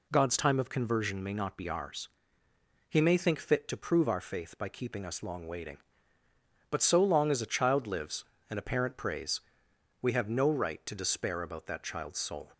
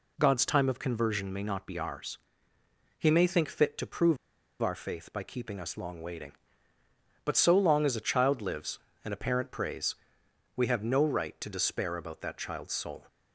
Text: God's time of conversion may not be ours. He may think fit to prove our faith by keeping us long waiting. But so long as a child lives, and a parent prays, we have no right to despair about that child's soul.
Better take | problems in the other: first | pauses between "prove" and "our"; at 4.1 s; 0.44 s long

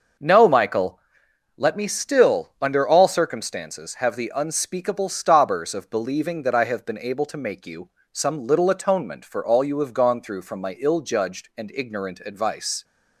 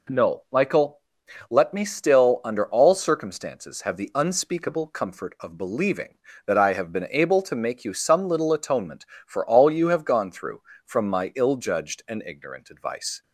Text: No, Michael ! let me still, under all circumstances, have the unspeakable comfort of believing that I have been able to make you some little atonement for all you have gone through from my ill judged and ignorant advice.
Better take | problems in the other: second | starts louder than the rest; until 1.7 s; 6 dB // says "stobbers" for "comfort"; at 5.0 s // pauses between "you" and "some"; slight; at 7.8 s; 0.22 s long

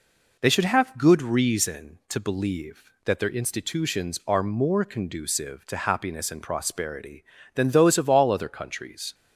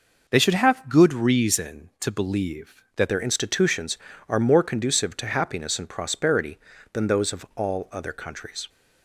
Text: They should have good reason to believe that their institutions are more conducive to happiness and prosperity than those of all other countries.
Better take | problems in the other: first | changes voice at "their"; from 3.0 s on; 5.6 s long

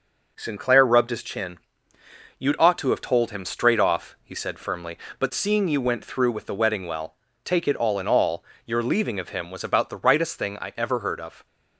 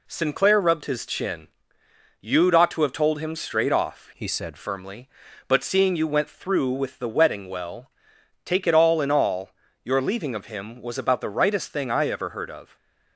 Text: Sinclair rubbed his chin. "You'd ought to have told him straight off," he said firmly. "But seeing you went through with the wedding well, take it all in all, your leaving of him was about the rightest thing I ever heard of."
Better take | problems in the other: first | changes voice from "he" to "said"; from 4.1 to 4.5 s; 0.4 s long

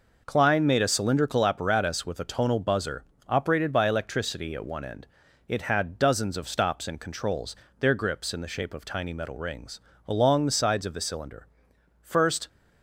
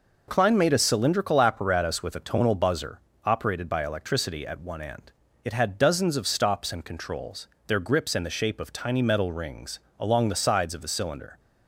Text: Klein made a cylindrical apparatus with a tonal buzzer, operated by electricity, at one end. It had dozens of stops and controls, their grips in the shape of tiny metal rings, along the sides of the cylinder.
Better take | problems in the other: second | goes on to say "First"; slight; from 12.0 s on; 0.46 s long

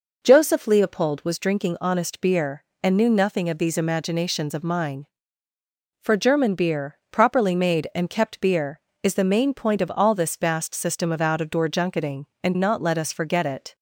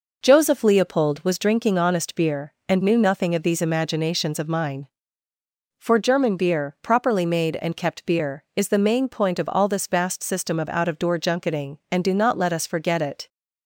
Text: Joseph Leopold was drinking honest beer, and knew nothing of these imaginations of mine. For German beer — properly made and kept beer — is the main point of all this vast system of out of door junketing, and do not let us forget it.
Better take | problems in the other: second | skips "do"; at 12.5 s

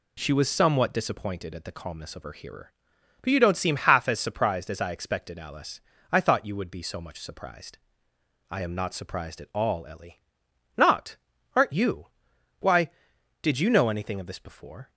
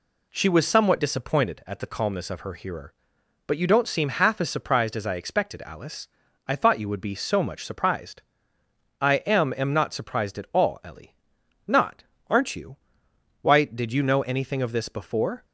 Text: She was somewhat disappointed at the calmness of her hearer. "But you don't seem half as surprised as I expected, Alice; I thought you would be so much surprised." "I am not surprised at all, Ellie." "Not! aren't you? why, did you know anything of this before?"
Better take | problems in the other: first | says "am" twice; at 9.5 s

